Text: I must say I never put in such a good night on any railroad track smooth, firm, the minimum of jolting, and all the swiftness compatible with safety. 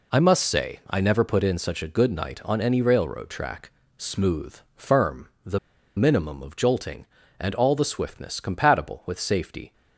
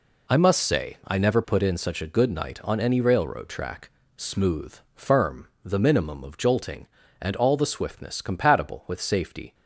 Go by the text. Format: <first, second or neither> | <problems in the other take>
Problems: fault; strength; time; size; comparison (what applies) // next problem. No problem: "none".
second | pauses between "track" and "smooth"; slight; at 3.7 s; 0.26 s long; slight in the second // pauses between "the" and "minimum"; at 5.5 s; 0.37 s long